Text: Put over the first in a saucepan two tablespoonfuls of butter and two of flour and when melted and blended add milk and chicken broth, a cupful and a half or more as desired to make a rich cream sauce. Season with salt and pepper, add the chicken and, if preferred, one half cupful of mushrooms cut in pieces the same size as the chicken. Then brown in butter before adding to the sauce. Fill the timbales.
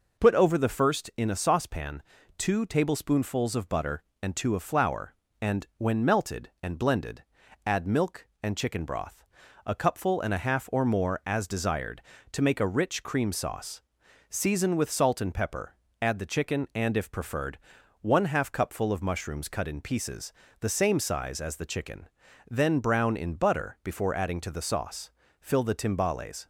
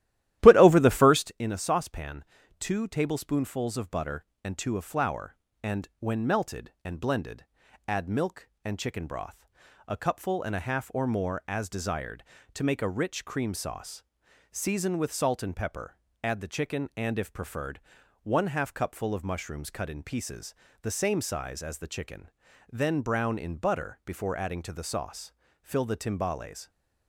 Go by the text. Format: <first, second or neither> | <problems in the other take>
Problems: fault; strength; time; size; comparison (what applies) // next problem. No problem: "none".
first | starts louder than the rest; strong; until 1.3 s; 13.5 dB // pauses between "saucepan" and "two"; slight; at 2.2 s; 0.36 s long; slight in the first // pauses between "blended" and "add"; at 7.4 s; 0.44 s long; also in the first // pauses between "pieces" and "the"; slight; at 20.5 s; 0.30 s long; slight in the first